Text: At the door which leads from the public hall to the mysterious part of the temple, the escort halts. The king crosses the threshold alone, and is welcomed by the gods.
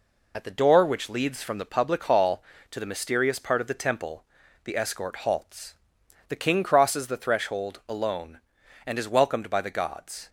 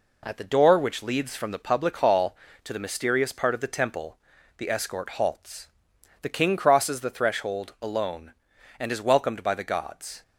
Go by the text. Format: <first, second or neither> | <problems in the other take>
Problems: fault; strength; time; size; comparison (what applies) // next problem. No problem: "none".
second | loses the start of "At"; at 0.3 s; 50 ms